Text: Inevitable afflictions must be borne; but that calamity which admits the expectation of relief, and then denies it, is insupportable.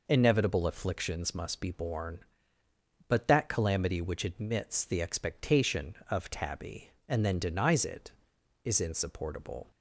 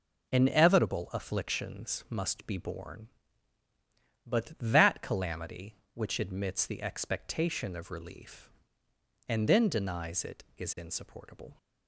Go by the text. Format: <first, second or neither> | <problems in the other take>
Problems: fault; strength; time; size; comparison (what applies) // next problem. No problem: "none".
second | says "tabby" for "relief"; at 6.2 s